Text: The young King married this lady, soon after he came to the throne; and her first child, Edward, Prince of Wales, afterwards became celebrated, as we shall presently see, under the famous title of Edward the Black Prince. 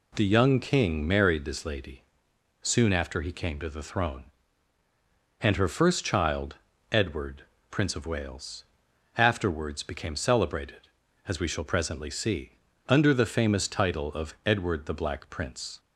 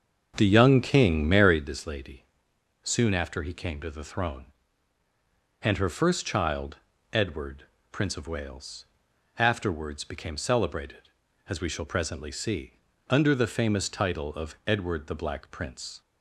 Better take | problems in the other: first | starts louder than the rest; until 1.7 s; 7 dB

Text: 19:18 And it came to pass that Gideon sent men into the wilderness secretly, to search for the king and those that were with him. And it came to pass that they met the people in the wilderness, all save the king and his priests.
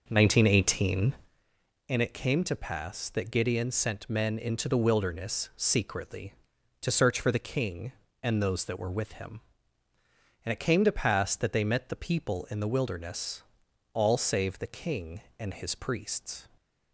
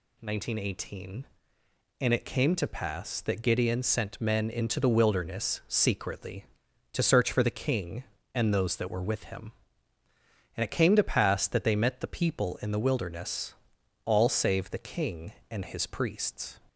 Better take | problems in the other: second | starts louder than the rest; noticeable; until 1.5 s; 5.5 dB

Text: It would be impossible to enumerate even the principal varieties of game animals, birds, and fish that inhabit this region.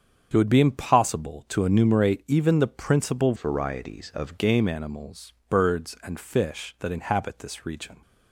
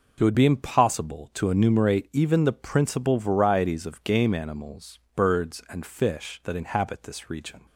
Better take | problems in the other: second | starts louder than the rest; strong; until 1.3 s; 7 dB // changes voice from "varieties" to "of"; from 3.3 to 4.3 s; 1.0 s long

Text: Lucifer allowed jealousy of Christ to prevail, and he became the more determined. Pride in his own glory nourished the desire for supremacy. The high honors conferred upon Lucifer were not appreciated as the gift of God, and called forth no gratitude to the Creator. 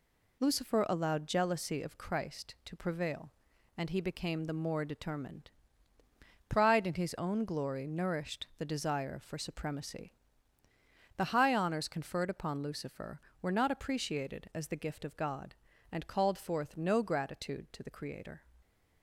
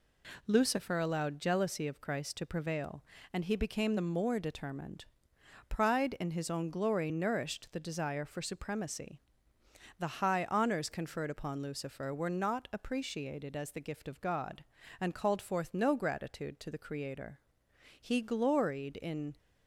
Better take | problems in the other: first | goes on to say "He gloried in"; from 17.9 s on; 1.3 s long

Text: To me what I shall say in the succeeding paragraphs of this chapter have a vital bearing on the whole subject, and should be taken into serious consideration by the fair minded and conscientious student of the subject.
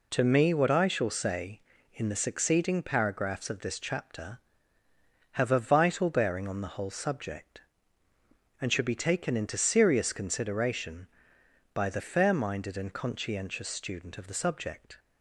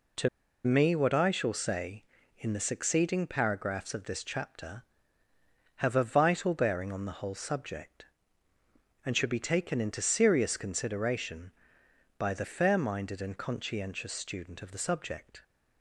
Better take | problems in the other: first | pauses between "To" and "me"; at 0.2 s; 0.36 s long

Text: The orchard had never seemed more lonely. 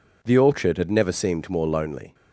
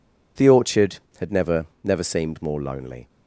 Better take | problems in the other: first | says "never" twice; at 1.8 s

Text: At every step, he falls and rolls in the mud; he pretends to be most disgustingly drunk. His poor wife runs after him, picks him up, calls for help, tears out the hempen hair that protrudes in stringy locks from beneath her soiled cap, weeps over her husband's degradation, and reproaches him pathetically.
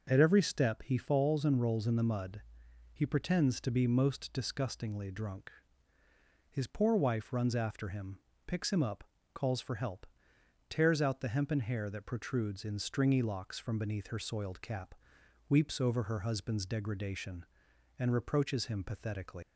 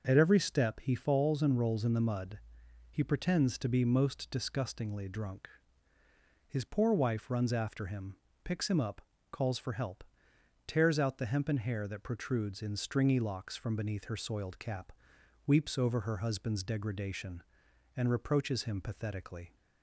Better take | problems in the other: second | leaves "pathetically" unfinished; at 19.4 s; 155 ms

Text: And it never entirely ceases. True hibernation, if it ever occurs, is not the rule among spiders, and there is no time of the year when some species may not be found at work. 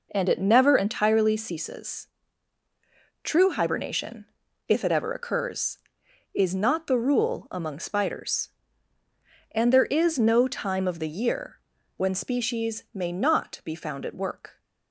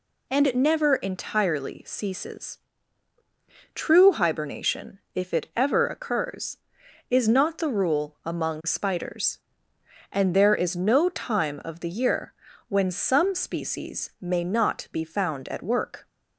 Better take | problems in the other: second | pauses between "year" and "when"; slight; at 11.5 s; 0.36 s long; slight in the second // skips "some"; at 12.1 s

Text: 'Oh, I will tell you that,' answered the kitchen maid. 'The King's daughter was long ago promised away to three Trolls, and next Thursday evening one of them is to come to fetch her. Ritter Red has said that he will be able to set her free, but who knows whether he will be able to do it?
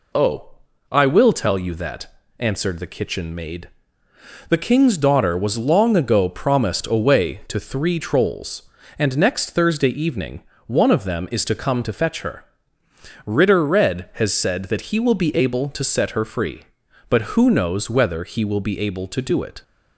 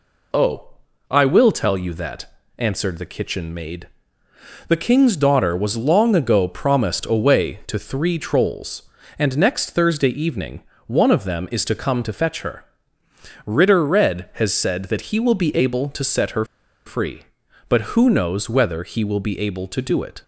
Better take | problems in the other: first | pauses between "evening" and "one"; slight; at 10.6 s; 0.24 s long; slight in the first // pauses between "her" and "free"; at 16.4 s; 0.40 s long

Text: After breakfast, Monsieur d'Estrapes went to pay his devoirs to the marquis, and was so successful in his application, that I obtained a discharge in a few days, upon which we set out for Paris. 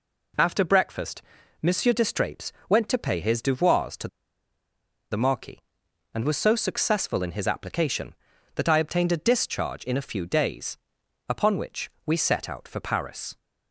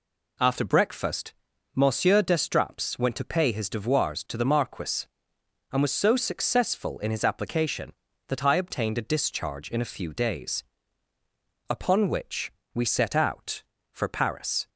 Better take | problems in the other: second | pauses between "d'Estrapes" and "went"; slight; at 2.5 s; 0.18 s long // pauses between "to" and "the"; at 4.0 s; 1.0 s long // pauses between "which" and "we"; slight; at 11.9 s; 0.16 s long; slight in the second

